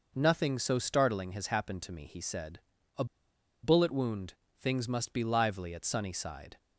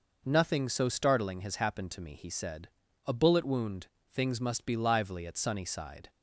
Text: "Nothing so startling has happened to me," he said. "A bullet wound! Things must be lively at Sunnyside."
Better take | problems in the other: second | pauses between "A" and "bullet"; noticeable; at 3.0 s; 0.58 s long

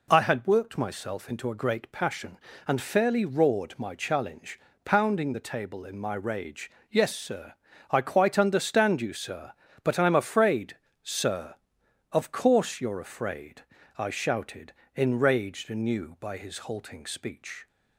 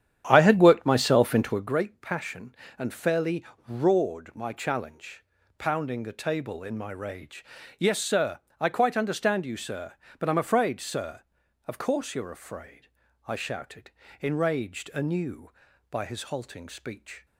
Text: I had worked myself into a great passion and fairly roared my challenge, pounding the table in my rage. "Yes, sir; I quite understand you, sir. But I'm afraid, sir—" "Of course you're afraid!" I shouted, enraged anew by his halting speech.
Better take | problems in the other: first | starts louder than the rest; strong; until 1.7 s; 9.5 dB // pauses between "fairly" and "roared"; slight; at 3.4 s; 0.24 s long

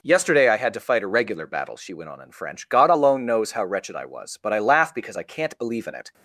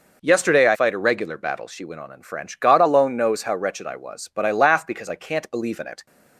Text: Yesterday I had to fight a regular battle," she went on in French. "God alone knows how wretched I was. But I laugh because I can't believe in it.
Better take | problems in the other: first | skips "had to"; at 0.7 s

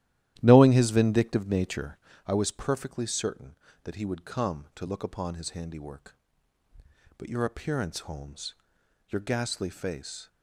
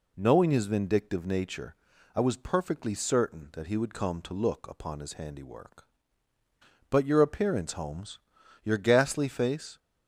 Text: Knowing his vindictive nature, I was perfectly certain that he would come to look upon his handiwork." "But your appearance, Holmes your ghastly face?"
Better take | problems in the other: second | starts louder than the rest; strong; until 2.2 s; 13 dB // pauses between "Holmes" and "your"; noticeable; at 8.5 s; 0.54 s long; also in the second

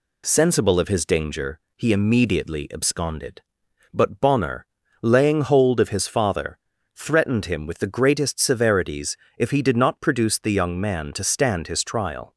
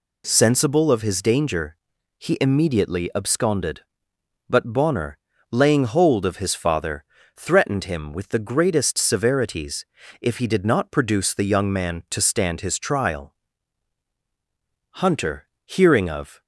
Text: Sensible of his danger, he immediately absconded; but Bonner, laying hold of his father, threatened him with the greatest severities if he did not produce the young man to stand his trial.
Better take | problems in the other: first | pauses between "severities" and "if"; slight; at 9.8 s; 0.36 s long; slight in the first // goes on to say "Hunter hearing of"; from 14.9 s on; 1.4 s long

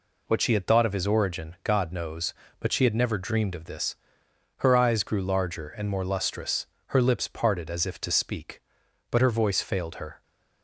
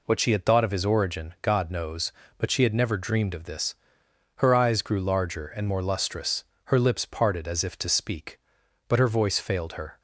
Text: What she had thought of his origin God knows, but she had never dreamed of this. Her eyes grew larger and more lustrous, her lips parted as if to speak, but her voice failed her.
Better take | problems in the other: neither | none

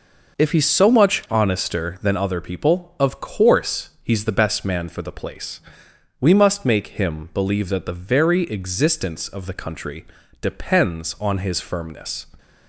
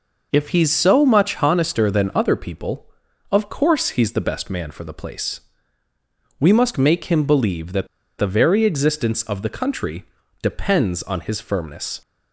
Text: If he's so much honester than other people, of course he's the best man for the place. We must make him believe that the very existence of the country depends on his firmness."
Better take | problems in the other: first | pauses between "that" and "the"; slight; at 7.8 s; 0.32 s long // pauses between "country" and "depends"; slight; at 10.0 s; 0.36 s long; also in the first

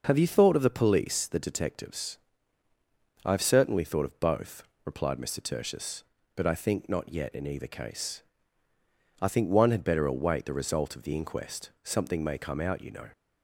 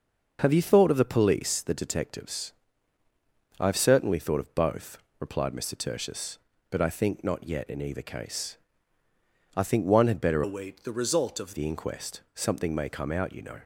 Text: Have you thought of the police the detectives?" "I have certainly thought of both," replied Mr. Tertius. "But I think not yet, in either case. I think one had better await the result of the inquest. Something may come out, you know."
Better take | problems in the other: first | starts louder than the rest; until 1.4 s; 6 dB // changes voice from "await" to "of"; from 10.4 to 11.5 s; 1.1 s long

